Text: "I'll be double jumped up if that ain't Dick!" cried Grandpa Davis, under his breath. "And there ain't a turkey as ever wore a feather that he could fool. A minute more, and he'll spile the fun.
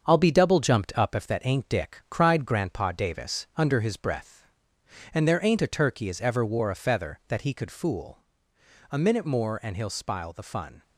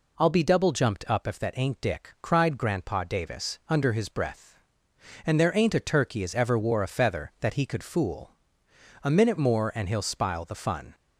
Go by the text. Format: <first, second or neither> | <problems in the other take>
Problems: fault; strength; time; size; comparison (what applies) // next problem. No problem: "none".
second | gets quieter; noticeable; throughout; 5 dB